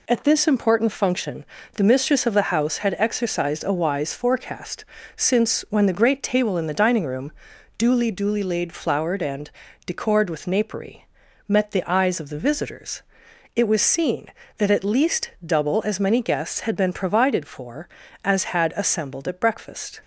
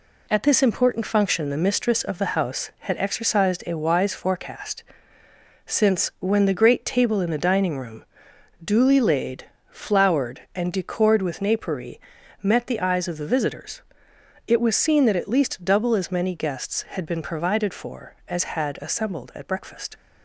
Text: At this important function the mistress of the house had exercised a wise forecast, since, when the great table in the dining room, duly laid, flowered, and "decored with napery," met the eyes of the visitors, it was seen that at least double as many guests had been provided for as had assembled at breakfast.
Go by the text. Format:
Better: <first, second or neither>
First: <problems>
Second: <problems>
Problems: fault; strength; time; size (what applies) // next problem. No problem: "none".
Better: second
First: pauses between "function" and "the"; slight; at 1.4 s; 0.34 s long // says "duly" twice; at 8.1 s // pauses between "and" and "decored"; at 9.4 s; 0.38 s long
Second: none